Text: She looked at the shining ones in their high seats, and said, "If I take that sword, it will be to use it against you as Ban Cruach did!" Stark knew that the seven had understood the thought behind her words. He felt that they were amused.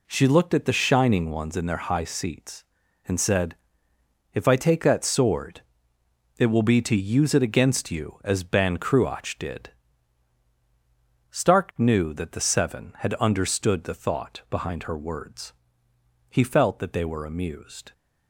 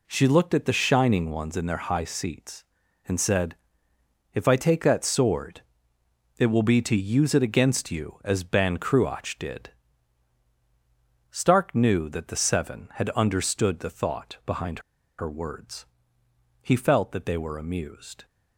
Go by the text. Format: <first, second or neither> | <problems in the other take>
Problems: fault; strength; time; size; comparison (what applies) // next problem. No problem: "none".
first | pauses between "behind" and "her"; at 14.8 s; 0.38 s long